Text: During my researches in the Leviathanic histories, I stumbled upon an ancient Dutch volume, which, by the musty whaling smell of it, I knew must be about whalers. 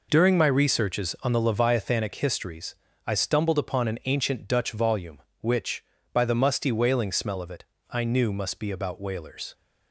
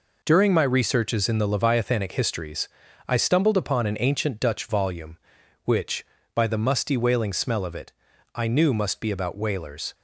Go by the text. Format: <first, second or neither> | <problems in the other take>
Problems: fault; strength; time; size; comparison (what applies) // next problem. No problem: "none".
second | says "on" for "in"; at 1.2 s